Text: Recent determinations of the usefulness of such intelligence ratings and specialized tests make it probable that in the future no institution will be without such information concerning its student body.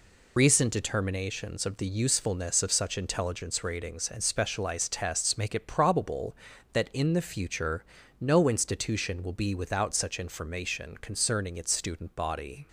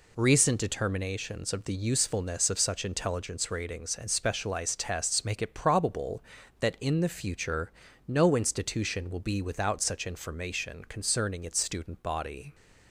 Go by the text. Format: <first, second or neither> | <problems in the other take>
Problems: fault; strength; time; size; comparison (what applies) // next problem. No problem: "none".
second | loses the start of "Recent"; at 0.3 s; 70 ms // pauses between "future" and "no"; slight; at 7.8 s; 0.34 s long; slight in the second